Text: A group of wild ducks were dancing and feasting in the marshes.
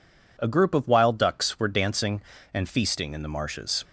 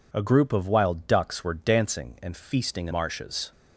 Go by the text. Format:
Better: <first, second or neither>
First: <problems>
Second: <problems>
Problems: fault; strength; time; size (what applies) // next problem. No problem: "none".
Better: first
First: none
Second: skips "the"; at 2.9 s